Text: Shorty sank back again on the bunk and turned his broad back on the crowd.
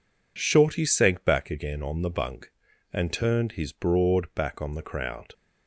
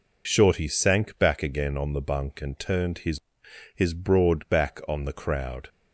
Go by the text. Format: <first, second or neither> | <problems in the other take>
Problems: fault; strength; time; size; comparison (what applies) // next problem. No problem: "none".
first | says "his" twice; at 3.7 s